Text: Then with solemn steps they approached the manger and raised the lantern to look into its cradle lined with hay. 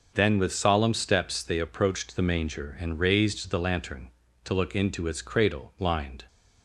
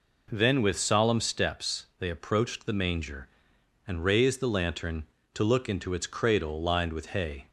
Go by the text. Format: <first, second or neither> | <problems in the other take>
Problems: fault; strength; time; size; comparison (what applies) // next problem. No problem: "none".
second | starts louder than the rest; until 1.1 s; 6.5 dB // stops before "with hay"; at 6.2 s